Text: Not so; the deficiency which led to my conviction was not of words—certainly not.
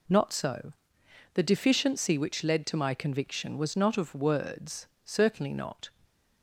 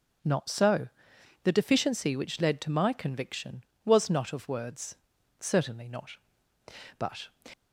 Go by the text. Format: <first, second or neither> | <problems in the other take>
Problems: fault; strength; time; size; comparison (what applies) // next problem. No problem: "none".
first | starts louder than the rest; until 1.7 s; 7 dB // goes on to say "But"; slight; from 6.9 s on; 0.30 s long